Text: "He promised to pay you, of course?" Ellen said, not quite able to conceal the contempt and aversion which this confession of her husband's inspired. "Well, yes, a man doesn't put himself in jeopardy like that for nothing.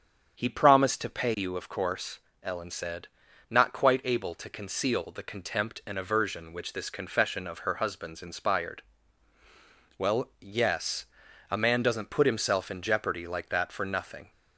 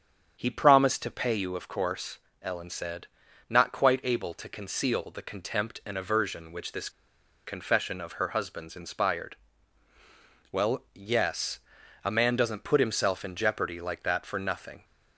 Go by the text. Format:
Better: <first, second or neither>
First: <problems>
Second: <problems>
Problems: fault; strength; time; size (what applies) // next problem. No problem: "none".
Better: first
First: starts louder than the rest; strong; until 1.4 s; 8 dB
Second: starts louder than the rest; strong; until 1.4 s; 7.5 dB // pauses between "this" and "confession"; noticeable; at 6.8 s; 0.57 s long